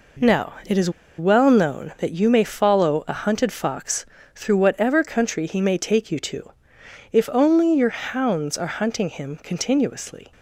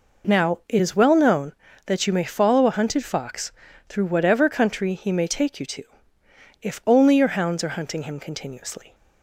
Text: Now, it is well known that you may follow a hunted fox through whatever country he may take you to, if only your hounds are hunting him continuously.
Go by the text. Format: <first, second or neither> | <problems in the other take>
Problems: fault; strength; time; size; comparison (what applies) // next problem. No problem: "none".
second | pauses between "is" and "well"; slight; at 0.8 s; 0.28 s long // pauses between "fox" and "through"; slight; at 4.0 s; 0.32 s long; also in the second